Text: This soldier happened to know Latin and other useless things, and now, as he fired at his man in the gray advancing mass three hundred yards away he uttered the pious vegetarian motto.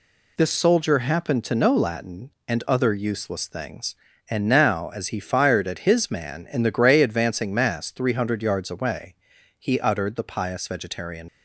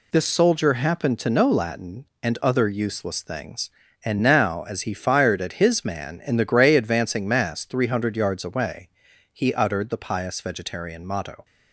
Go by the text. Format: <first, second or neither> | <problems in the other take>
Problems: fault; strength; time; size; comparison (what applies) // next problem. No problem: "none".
second | pauses between "away" and "he"; at 9.1 s; 0.44 s long; also in the second // stops before "motto"; at 11.2 s